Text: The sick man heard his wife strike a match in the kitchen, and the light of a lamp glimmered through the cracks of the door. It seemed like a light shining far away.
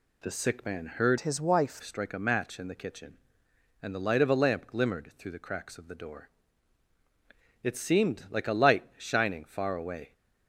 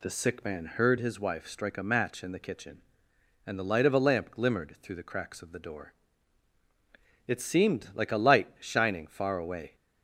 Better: second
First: changes voice from "his" to "wife"; from 1.1 to 1.8 s; 0.7 s long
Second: none

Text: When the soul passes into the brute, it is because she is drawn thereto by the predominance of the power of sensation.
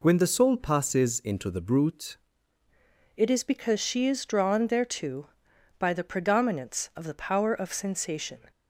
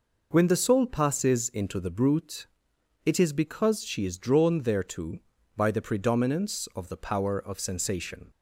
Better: second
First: changes voice at "it"; from 3.1 s on; 5.4 s long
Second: none

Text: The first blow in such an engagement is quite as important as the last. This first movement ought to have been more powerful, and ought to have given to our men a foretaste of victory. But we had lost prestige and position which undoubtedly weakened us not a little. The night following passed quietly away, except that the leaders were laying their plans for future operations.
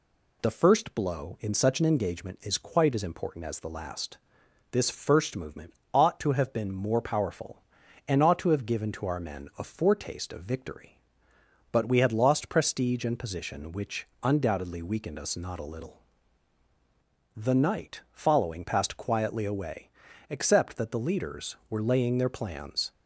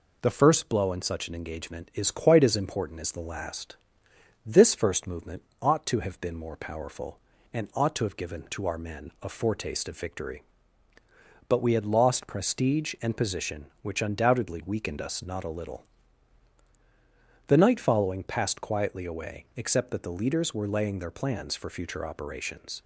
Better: second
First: pauses between "movement" and "ought"; slight; at 5.7 s; 0.20 s long // pauses between "which" and "undoubtedly"; slight; at 14.0 s; 0.16 s long // stops before "for future operations"; at 22.9 s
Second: pauses between "movement" and "ought"; slight; at 5.4 s; 0.18 s long

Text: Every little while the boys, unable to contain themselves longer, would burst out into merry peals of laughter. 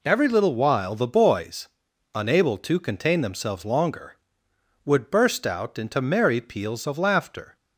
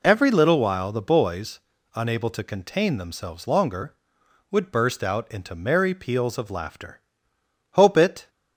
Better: first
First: none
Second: goes on to say "Hope it"; from 7.7 s on; 0.58 s long

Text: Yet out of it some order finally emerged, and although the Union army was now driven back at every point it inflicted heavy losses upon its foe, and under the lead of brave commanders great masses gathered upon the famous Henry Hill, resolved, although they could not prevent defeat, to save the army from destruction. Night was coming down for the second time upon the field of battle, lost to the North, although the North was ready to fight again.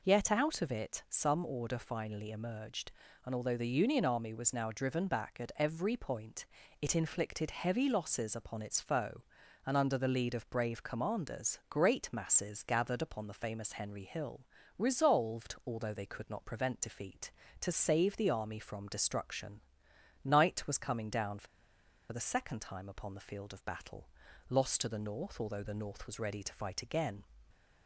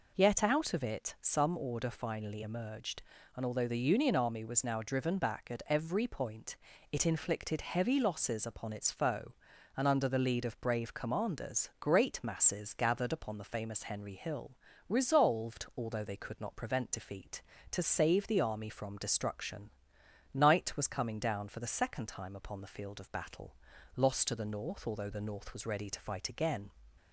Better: second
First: pauses between "point" and "it"; slight; at 6.4 s; 0.34 s long // pauses between "for" and "the"; noticeable; at 21.4 s; 0.65 s long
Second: pauses between "point" and "it"; slight; at 6.5 s; 0.34 s long

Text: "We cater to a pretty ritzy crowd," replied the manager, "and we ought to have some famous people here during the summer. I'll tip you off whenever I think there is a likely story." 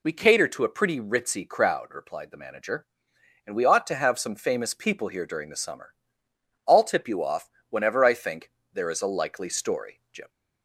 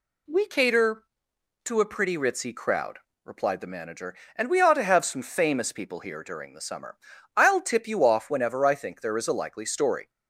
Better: second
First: pauses between "off" and "whenever"; slight; at 7.5 s; 0.18 s long // pauses between "think" and "there"; slight; at 8.5 s; 0.20 s long // goes on to say "Jim"; slight; from 10.1 s on; 0.16 s long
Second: none

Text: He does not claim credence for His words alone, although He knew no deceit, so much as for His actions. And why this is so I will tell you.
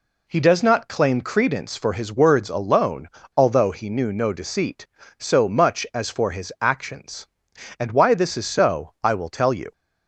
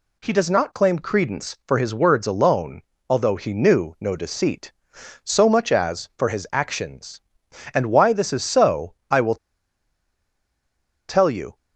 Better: first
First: none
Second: pauses between "will" and "tell"; strong; at 9.3 s; 1.7 s long

